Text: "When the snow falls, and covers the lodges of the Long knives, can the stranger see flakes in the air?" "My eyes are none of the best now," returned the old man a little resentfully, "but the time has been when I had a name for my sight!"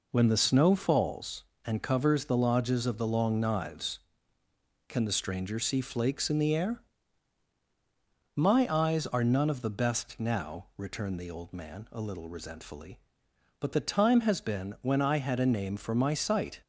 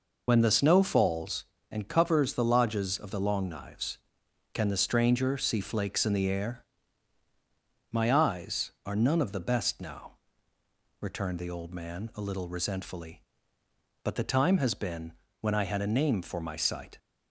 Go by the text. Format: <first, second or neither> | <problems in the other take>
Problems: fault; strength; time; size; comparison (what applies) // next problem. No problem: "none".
first | loses the start of "When"; at 0.2 s; 65 ms // pauses between "been" and "when"; slight; at 15.1 s; 0.26 s long